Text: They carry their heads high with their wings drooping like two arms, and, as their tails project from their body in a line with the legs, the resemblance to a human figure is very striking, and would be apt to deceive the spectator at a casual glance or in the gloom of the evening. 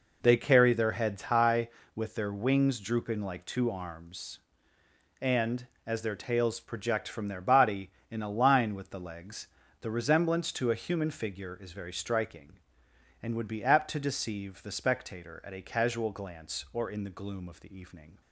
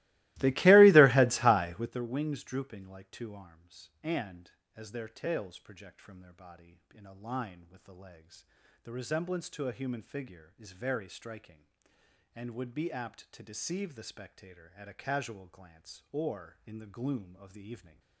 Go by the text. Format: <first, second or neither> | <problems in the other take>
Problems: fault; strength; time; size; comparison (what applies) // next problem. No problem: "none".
first | starts louder than the rest; strong; until 2.0 s; 19.5 dB